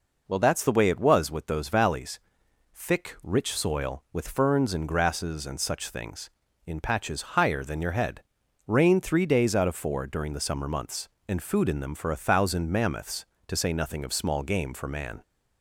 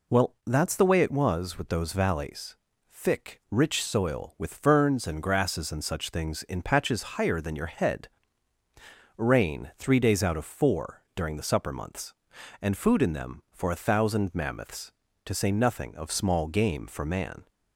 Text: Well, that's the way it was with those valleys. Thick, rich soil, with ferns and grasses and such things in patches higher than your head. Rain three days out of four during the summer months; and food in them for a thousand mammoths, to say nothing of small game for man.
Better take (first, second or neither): first